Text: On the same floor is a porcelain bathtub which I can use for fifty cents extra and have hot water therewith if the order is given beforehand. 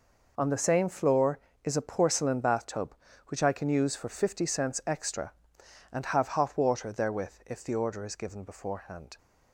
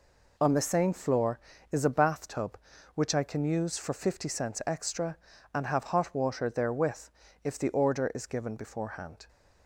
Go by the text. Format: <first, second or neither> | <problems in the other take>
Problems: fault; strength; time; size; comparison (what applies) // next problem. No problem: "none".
first | skips "porcelain"; at 1.8 s // pauses between "therewith" and "if"; slight; at 7.0 s; 0.34 s long